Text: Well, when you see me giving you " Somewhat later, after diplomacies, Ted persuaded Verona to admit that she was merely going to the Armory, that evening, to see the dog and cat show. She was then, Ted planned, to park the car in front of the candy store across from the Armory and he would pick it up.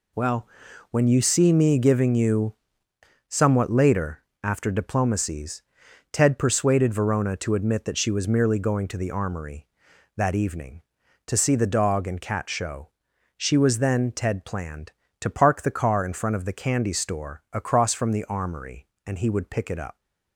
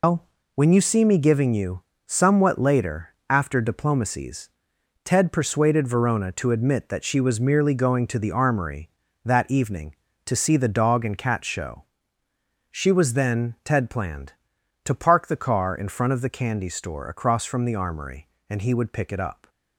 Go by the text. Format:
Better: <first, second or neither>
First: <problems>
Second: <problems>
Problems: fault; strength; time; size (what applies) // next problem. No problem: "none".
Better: first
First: none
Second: loses the start of "Well"; at 0.0 s; 150 ms